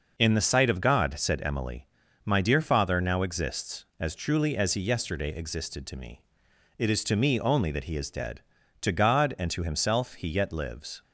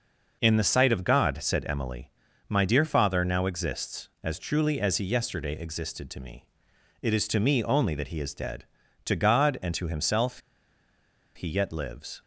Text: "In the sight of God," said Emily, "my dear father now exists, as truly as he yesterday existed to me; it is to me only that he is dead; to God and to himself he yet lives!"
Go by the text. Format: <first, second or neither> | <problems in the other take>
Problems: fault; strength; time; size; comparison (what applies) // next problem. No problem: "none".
first | pauses between "himself" and "he"; noticeable; at 10.3 s; 0.96 s long